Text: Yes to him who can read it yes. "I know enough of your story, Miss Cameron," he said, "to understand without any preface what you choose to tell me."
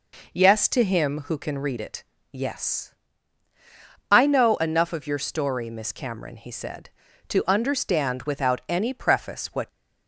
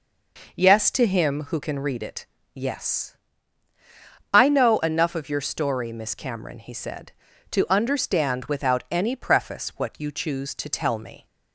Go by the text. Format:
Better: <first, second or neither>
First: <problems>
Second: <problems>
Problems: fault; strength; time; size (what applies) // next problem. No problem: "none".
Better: second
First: pauses between "it" and "yes"; slight; at 2.0 s; 0.28 s long // stops before "you choose to tell me"; at 9.6 s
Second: pauses between "it" and "yes"; slight; at 2.2 s; 0.28 s long